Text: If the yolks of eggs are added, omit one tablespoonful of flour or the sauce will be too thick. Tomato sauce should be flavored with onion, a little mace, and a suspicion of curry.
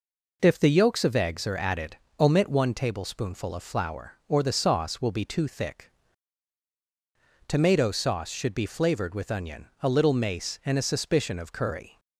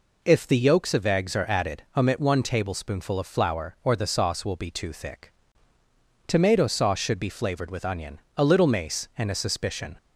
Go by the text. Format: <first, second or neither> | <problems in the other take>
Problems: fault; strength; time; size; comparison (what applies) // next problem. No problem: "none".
first | stops before "of curry"; at 9.9 s